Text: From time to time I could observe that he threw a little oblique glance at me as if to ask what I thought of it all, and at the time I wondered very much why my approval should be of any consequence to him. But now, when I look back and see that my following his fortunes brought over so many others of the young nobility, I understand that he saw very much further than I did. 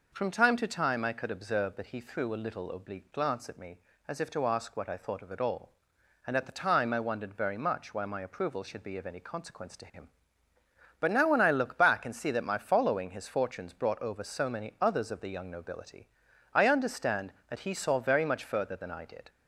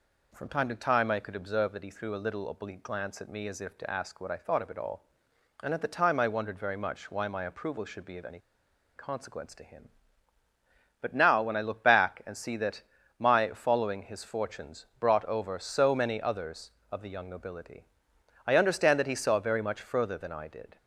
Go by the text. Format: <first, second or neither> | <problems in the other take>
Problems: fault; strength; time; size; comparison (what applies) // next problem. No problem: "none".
first | pauses between "any" and "consequence"; noticeable; at 8.3 s; 0.57 s long // pauses between "that" and "my"; slight; at 12.8 s; 0.34 s long